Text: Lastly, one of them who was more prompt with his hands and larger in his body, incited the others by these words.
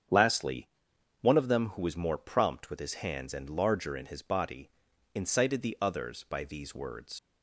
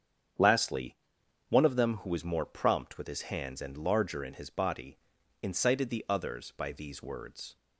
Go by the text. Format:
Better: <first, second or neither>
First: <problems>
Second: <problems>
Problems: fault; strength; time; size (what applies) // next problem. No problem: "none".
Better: second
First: starts louder than the rest; strong; until 1.6 s; 7.5 dB // leaves "words" unfinished; at 7.1 s; 95 ms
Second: starts louder than the rest; strong; until 1.8 s; 7.5 dB